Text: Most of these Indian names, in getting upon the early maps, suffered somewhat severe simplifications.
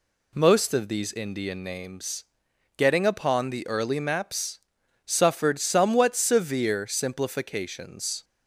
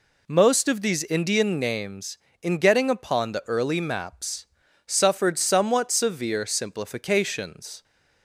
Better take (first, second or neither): second